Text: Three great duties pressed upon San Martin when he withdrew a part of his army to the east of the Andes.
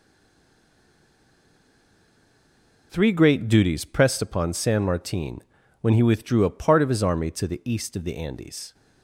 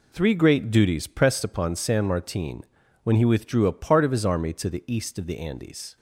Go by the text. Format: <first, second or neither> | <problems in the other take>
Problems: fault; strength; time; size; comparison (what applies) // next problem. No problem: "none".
second | stays silent before the first word; strong; until 2.9 s; 2.9 s long // pauses between "Martin" and "when"; at 5.4 s; 0.38 s long; also in the second